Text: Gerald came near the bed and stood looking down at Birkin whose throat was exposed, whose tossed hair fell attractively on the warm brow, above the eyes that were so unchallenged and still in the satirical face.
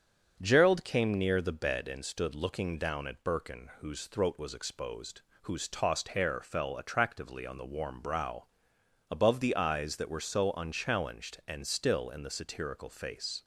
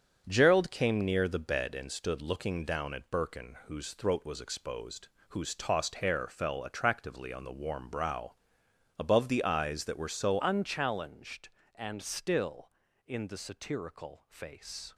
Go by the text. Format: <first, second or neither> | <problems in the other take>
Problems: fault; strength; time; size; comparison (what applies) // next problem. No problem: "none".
first | starts louder than the rest; until 1.3 s; 7 dB; also in the first // changes voice at "unchallenged"; from 10.4 s on; 4.5 s long